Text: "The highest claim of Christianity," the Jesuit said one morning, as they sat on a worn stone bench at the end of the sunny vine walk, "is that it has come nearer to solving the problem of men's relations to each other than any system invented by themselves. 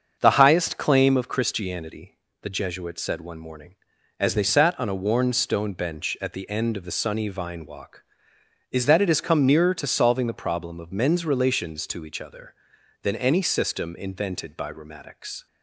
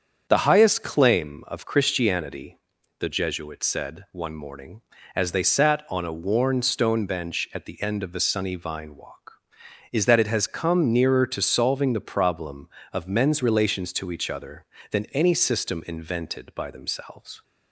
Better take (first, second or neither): second